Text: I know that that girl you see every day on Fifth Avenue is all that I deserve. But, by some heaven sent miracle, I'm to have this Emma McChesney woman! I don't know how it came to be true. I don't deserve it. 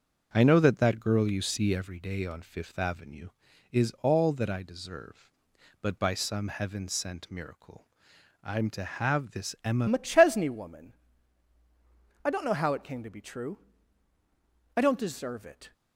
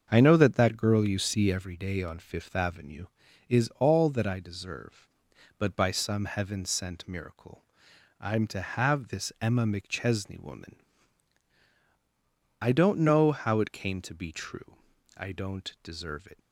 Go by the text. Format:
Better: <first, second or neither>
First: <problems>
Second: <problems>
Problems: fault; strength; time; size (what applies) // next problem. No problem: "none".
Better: second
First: starts louder than the rest; until 1.3 s; 6.5 dB // changes voice at "McChesney"; from 9.8 s on; 5.9 s long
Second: starts louder than the rest; until 1.1 s; 6.5 dB